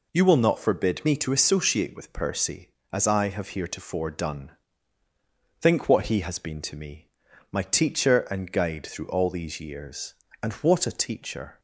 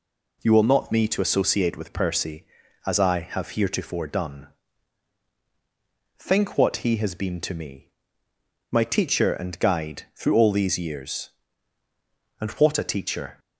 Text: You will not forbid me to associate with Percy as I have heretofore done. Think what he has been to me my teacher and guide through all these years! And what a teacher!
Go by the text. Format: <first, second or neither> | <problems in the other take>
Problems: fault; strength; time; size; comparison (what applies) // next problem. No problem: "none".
first | skips "forbid"; at 0.9 s // pauses between "me" and "my"; noticeable; at 7.8 s; 0.84 s long; also in the first